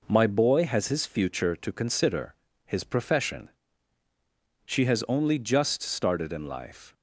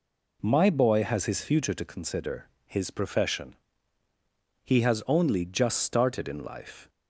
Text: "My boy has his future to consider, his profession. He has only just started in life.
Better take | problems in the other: second | says "She" for "He"; at 4.6 s

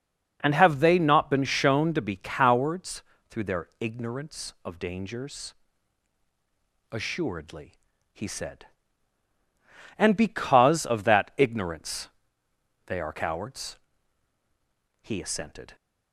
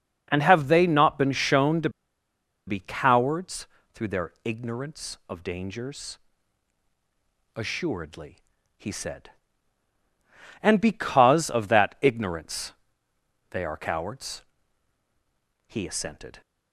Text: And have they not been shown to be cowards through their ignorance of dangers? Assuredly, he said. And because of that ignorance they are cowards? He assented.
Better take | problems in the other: first | pauses between "to" and "be"; noticeable; at 1.8 s; 0.78 s long // pauses between "cowards" and "through"; slight; at 3.6 s; 0.26 s long; slight in the first // pauses between "ignorance" and "they"; noticeable; at 12.7 s; 0.78 s long; noticeable in the first

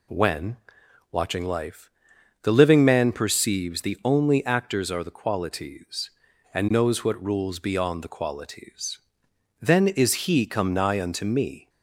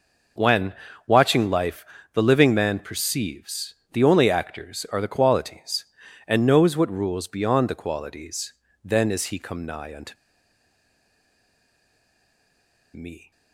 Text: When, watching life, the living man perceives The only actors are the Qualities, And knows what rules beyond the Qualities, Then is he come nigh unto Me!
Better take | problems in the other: first | pauses between "perceives" and "The"; slight; at 3.7 s; 0.20 s long // pauses between "unto" and "Me"; strong; at 10.1 s; 2.8 s long

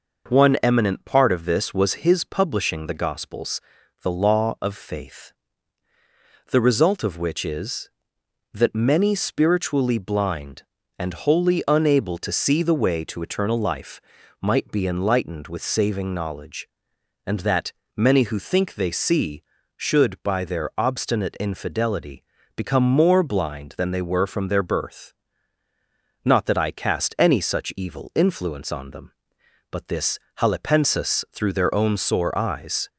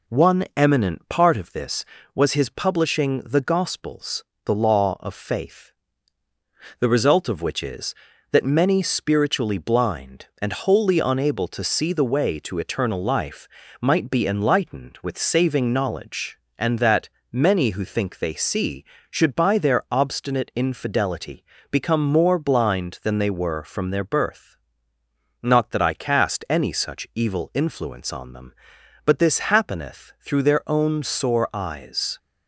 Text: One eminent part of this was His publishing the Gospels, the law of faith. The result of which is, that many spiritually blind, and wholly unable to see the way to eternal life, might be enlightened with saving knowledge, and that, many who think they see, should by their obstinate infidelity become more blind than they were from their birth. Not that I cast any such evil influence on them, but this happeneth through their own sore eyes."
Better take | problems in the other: second | pauses between "infidelity" and "become"; slight; at 22.2 s; 0.32 s long; slight in the second // says "halepensis" for "happeneth"; at 30.3 s

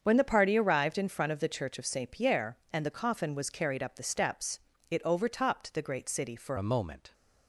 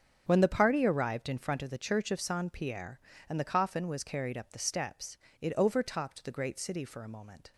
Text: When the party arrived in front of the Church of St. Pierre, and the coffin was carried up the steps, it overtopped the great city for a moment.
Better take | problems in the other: second | starts louder than the rest; strong; until 1.0 s; 7 dB; strong in the second // changes voice at "a"; from 6.5 s on; 0.6 s long

